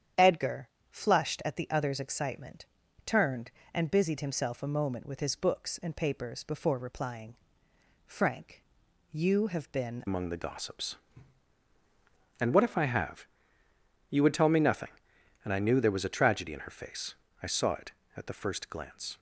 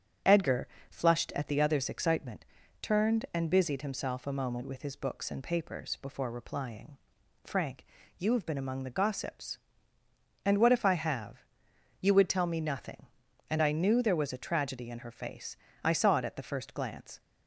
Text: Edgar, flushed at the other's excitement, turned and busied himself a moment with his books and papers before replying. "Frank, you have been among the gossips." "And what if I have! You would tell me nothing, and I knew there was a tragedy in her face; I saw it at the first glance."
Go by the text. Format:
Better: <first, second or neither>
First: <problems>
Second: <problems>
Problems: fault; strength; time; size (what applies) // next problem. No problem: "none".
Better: second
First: starts louder than the rest; strong; until 1.3 s; 9 dB // changes voice at "among"; from 10.0 s on; 9.1 s long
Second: starts louder than the rest; strong; until 1.5 s; 7 dB